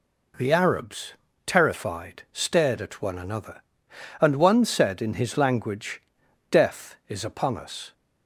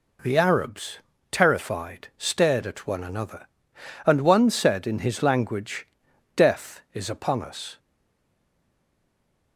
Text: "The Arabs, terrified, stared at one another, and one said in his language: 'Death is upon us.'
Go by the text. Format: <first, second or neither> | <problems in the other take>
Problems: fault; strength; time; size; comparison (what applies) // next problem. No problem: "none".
first | stays silent after the last word; noticeable; from 7.7 s on; 1.8 s long